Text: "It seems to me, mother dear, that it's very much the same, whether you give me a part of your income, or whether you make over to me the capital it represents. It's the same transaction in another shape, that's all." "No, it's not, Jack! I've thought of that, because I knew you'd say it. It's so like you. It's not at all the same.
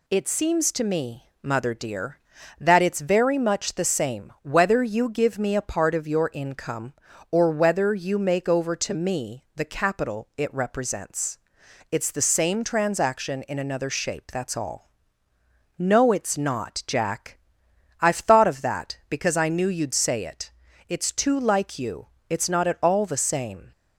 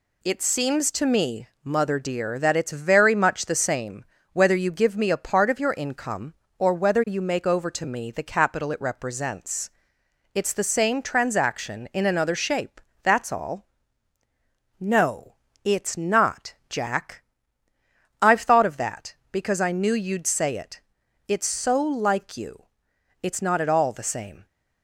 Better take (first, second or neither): second